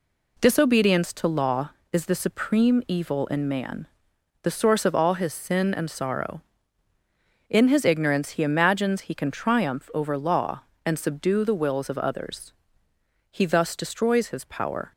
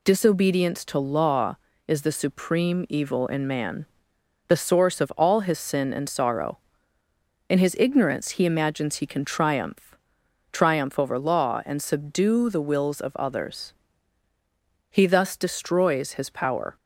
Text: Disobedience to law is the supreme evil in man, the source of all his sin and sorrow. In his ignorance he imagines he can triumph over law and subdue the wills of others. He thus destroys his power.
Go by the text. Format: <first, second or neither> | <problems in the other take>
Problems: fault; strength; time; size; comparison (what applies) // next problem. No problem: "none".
first | says "triumph" twice; at 10.5 s